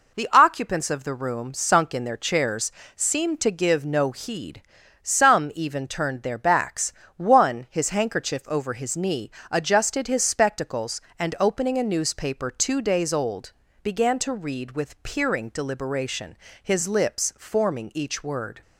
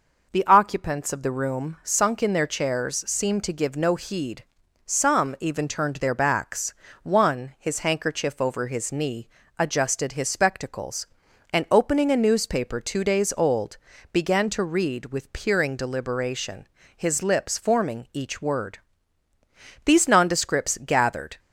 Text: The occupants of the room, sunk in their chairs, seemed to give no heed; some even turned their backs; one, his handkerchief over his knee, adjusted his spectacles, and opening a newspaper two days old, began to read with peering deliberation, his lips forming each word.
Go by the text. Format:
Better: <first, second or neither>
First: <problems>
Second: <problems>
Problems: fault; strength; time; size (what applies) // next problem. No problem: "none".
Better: first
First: none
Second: goes on to say "These nondescripts gathered"; from 19.8 s on; 1.5 s long